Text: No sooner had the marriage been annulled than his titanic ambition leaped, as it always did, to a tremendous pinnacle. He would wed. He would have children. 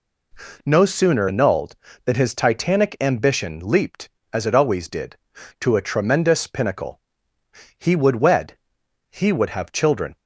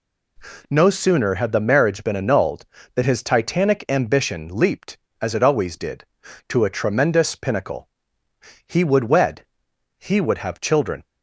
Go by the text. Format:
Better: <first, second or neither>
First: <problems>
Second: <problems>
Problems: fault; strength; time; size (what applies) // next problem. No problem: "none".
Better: second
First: skips "had the marriage been"; at 1.2 s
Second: none